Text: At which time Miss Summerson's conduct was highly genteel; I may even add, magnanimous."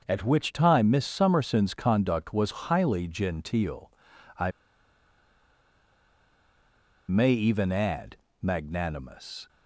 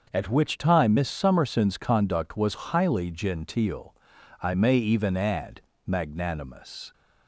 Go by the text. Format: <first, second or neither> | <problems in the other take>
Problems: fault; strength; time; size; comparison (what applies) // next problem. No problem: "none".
second | starts louder than the rest; until 1.0 s; 6.5 dB; also in the second // pauses between "I" and "may"; strong; at 4.5 s; 2.5 s long